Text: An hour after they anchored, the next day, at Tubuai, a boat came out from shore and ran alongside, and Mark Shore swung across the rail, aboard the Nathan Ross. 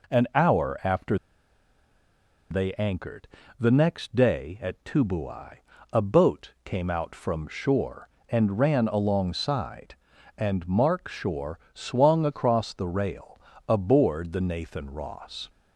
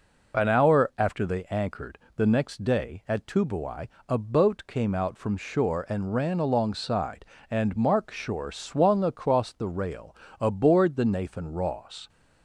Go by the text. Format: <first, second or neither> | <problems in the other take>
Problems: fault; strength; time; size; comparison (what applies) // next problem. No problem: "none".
second | pauses between "after" and "they"; strong; at 1.1 s; 1.3 s long // pauses between "Shore" and "swung"; slight; at 11.5 s; 0.16 s long